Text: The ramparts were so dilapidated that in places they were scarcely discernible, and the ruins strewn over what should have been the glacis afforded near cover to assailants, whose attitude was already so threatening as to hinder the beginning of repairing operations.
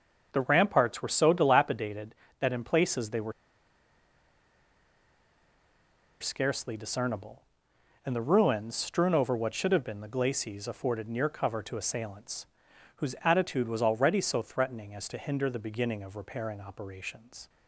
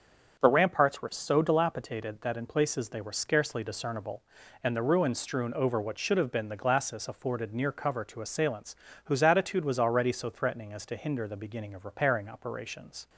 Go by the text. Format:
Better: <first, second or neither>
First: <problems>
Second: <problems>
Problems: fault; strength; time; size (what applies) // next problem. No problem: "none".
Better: second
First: starts louder than the rest; until 1.3 s; 6.5 dB // pauses between "were" and "scarcely"; strong; at 3.3 s; 2.8 s long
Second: starts louder than the rest; strong; until 1.4 s; 7 dB